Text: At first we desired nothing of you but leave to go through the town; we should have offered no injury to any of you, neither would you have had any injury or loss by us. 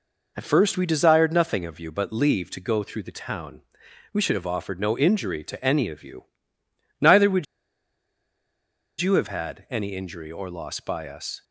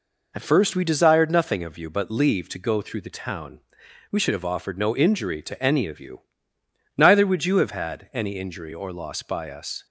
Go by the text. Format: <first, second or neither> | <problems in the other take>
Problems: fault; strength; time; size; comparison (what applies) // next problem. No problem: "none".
second | pauses between "would" and "you"; strong; at 7.4 s; 1.5 s long